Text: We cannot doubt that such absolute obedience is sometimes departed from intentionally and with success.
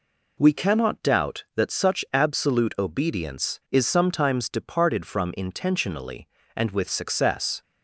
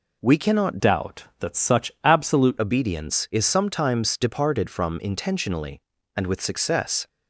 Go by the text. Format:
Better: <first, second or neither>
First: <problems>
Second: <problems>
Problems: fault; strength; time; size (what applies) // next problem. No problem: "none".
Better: first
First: none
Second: changes voice from "doubt" to "absolute"; from 0.8 to 2.5 s; 1.7 s long